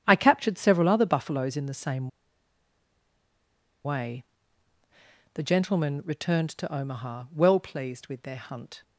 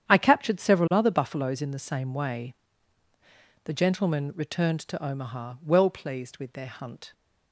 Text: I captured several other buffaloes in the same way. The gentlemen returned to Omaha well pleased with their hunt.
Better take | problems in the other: second | starts louder than the rest; strong; until 1.0 s; 9.5 dB; strong in the second // pauses between "same" and "way"; strong; at 2.0 s; 1.7 s long

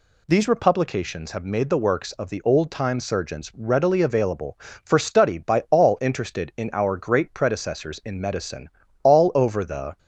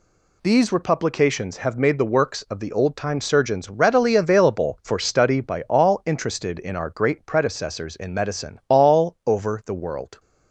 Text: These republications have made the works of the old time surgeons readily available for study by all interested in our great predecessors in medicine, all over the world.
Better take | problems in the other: second | stops before "world"; at 9.9 s

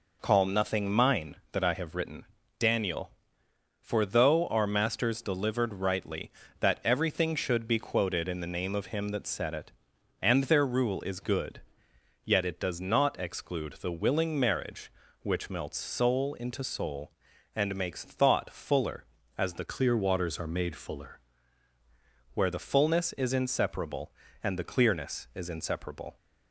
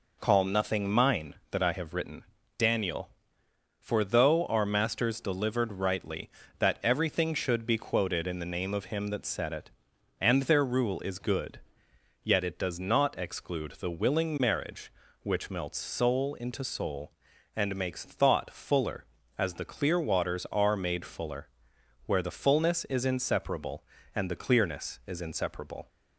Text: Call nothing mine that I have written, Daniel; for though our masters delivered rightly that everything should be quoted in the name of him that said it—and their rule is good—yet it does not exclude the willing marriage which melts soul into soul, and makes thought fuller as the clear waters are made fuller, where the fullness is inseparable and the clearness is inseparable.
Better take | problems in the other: second | changes voice from "clear" to "fuller"; from 19.6 to 21.2 s; 1.6 s long

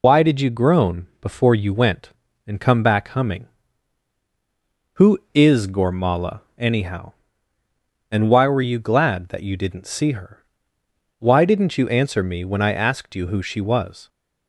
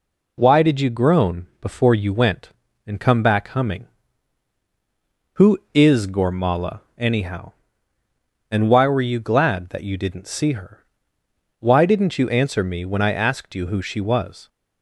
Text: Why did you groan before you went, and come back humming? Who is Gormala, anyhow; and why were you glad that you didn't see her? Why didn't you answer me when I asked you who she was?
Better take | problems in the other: second | loses the start of "Why"; at 0.0 s; 60 ms

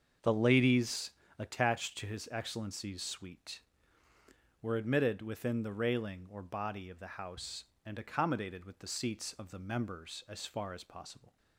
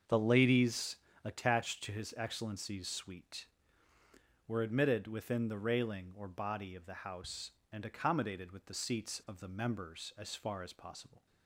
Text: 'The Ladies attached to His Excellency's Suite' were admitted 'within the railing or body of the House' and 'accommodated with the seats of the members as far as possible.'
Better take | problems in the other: neither | starts louder than the rest; the same in both // pauses between "Ladies" and "attached"; slight; the same in both

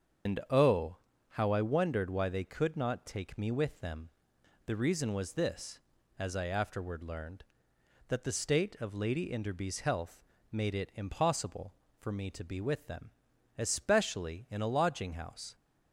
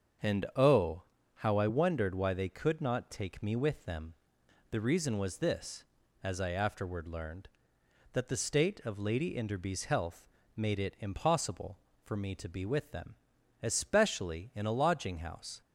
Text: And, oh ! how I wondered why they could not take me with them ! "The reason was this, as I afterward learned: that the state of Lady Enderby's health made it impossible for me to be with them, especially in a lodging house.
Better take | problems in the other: second | loses the start of "And"; at 0.2 s; 100 ms // starts louder than the rest; strong; until 1.7 s; 7 dB; strong in the second // pauses between "health" and "made"; slight; at 10.2 s; 0.30 s long; slight in the second

